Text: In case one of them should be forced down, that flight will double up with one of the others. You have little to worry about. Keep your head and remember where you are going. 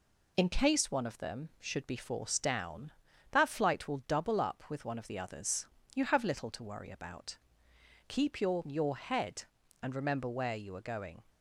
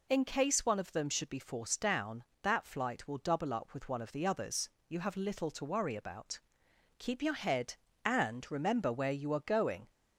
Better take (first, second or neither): second